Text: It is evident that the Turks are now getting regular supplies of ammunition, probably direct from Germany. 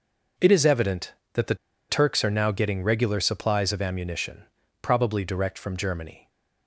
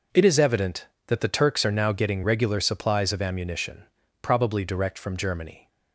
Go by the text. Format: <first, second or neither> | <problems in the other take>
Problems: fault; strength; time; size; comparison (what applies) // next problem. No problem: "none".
second | pauses between "the" and "Turks"; slight; at 1.5 s; 0.34 s long